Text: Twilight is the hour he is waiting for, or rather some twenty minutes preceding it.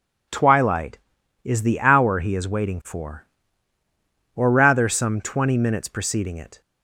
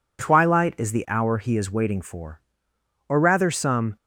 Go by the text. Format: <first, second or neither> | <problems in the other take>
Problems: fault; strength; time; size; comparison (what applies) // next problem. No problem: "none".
first | stops before "twenty minutes preceding it"; at 3.9 s